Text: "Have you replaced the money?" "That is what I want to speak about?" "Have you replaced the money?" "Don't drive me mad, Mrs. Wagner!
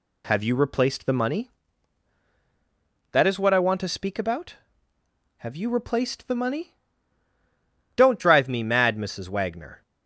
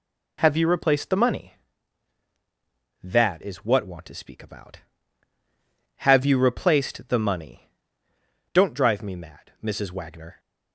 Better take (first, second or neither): first